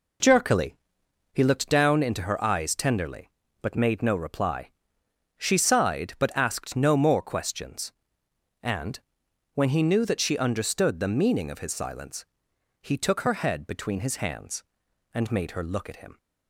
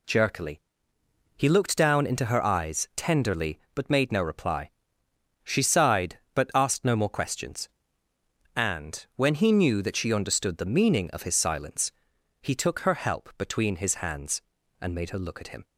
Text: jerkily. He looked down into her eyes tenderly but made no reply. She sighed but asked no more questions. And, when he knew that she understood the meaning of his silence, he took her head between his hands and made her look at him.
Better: first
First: none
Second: says "help" for "head"; at 12.9 s

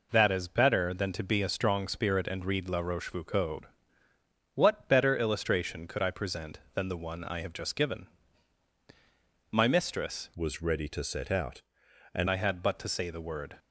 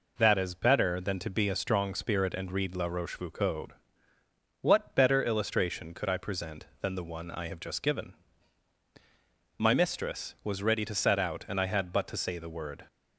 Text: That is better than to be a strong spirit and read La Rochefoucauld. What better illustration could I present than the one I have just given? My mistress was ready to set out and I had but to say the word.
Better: second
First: changes voice from "was" to "and"; from 10.3 to 12.2 s; 1.9 s long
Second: none

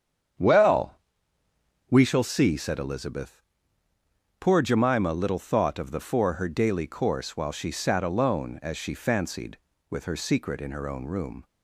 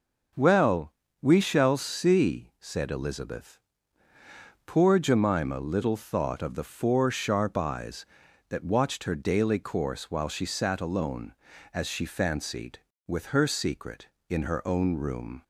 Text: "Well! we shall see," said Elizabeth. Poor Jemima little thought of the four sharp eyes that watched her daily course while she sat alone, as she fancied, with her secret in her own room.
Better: second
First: starts louder than the rest; strong; until 2.3 s; 8 dB // skips "sharp eyes that watched"; at 6.3 s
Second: none

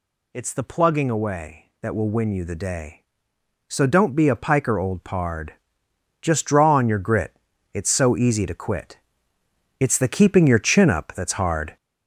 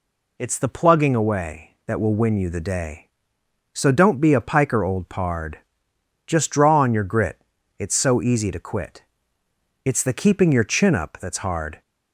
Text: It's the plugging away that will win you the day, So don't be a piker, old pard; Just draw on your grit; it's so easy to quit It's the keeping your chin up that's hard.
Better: second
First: gets louder; noticeable; throughout; 5.5 dB // pauses between "quit" and "It's"; noticeable; at 8.9 s; 0.82 s long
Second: pauses between "quit" and "It's"; noticeable; at 9.0 s; 0.82 s long

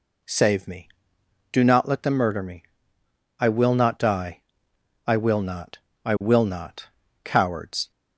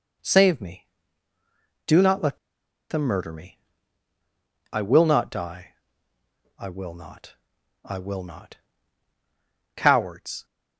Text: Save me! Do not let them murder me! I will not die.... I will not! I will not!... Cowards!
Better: first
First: none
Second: pauses between "let" and "them"; noticeable; at 2.3 s; 0.52 s long

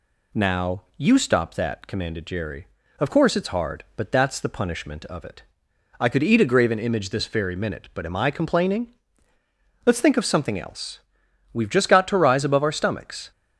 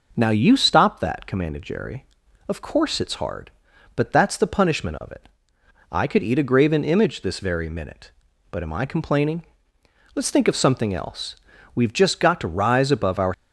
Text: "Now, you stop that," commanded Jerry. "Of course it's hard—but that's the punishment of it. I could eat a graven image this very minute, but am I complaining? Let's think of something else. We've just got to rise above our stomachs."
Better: first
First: none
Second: stops before "stomachs"; at 13.3 s

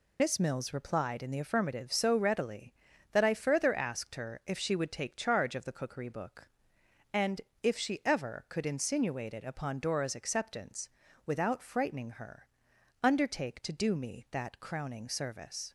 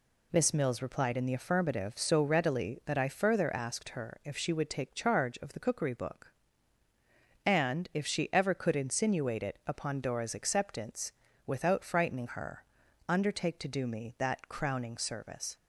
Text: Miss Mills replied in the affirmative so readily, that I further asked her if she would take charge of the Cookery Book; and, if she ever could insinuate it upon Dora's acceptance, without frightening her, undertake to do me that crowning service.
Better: second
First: loses the start of "Miss"; at 0.1 s; 55 ms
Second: none

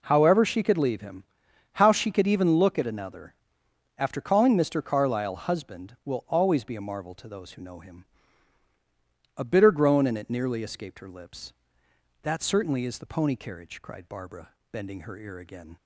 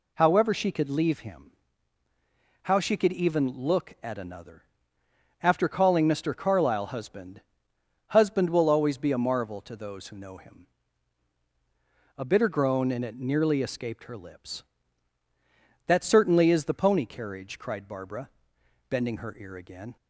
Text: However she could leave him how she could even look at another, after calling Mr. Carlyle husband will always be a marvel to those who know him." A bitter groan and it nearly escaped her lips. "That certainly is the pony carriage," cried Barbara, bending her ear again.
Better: first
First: pauses between "him" and "how"; noticeable; at 1.2 s; 0.50 s long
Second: pauses between "him" and "how"; at 1.4 s; 1.1 s long // says "husband" twice; at 8.0 s

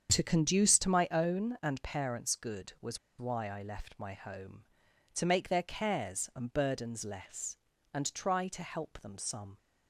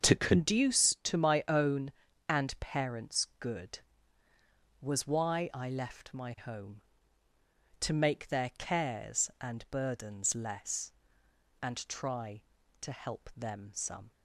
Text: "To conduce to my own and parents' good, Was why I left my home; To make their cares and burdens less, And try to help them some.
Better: second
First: starts louder than the rest; strong; until 1.1 s; 7.5 dB // pauses between "Was" and "why"; slight; at 2.9 s; 0.21 s long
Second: starts louder than the rest; until 1.1 s; 7 dB

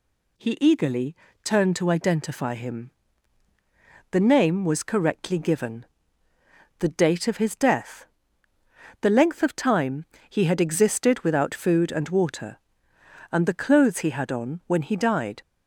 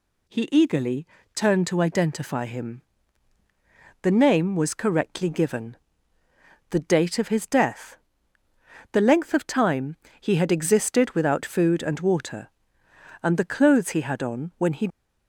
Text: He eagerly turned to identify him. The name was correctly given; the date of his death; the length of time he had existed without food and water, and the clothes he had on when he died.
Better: first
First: pauses between "eagerly" and "turned"; slight; at 1.1 s; 0.28 s long // pauses between "time" and "he"; slight; at 10.0 s; 0.24 s long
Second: pauses between "eagerly" and "turned"; slight; at 1.0 s; 0.28 s long // pauses between "time" and "he"; slight; at 9.9 s; 0.24 s long // stops before "died"; at 14.8 s

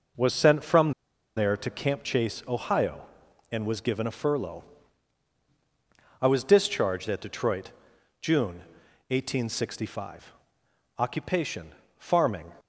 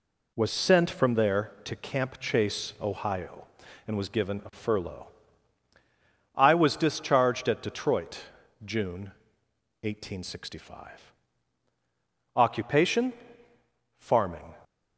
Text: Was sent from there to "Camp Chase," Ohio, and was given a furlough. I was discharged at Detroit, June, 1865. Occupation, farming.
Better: second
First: pauses between "from" and "there"; at 0.9 s; 0.45 s long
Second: none

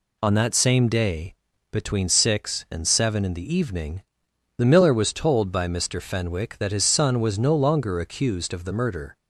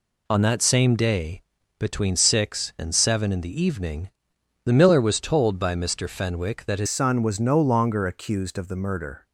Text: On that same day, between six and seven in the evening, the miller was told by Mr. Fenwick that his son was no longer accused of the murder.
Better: first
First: none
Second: changes voice at "son"; from 6.8 s on; 2.4 s long

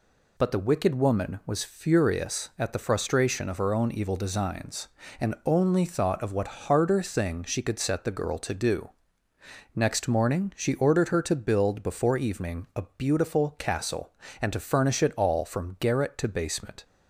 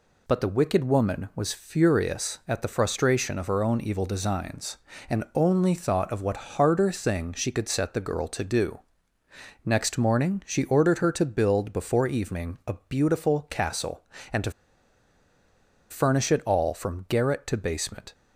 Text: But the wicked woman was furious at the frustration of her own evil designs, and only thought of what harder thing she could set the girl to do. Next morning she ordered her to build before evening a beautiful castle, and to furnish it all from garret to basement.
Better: first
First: none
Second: pauses between "to" and "furnish"; strong; at 14.5 s; 1.4 s long

